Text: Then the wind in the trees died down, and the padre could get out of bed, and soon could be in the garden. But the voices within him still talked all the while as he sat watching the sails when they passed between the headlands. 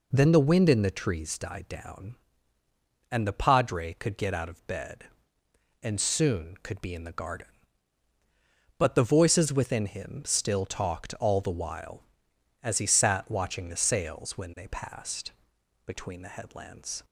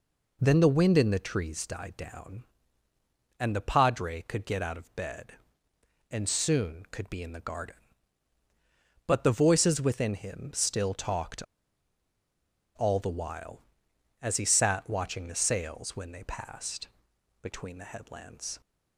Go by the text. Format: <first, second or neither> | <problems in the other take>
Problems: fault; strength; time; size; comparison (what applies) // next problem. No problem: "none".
first | pauses between "talked" and "all"; strong; at 11.4 s; 1.3 s long // pauses between "passed" and "between"; noticeable; at 16.8 s; 0.52 s long; noticeable in the first